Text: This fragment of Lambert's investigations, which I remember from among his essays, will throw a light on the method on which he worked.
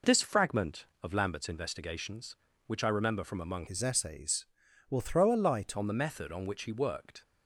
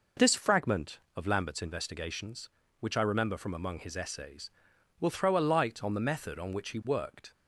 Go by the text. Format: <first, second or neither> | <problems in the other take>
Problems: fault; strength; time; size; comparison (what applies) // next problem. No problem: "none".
second | changes voice from "his" to "light"; from 3.6 to 5.7 s; 2.1 s long